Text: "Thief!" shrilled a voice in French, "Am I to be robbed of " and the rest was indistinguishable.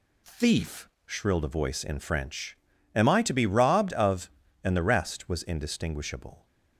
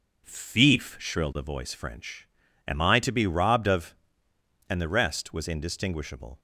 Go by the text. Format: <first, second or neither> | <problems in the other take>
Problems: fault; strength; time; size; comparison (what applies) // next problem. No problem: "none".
first | starts louder than the rest; until 1.2 s; 6.5 dB // skips "in"; at 1.7 s